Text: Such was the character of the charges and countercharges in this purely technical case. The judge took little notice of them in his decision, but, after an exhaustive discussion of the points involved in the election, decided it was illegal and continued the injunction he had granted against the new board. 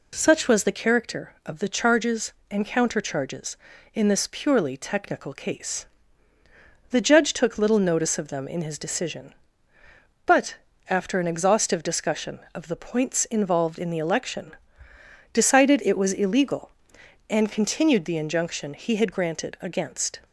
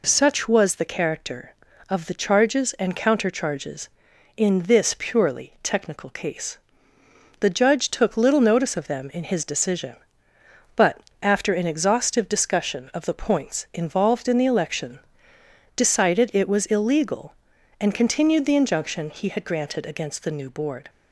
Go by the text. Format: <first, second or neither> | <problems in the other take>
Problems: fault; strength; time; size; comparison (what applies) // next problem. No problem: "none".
second | stops before "the new board"; at 20.2 s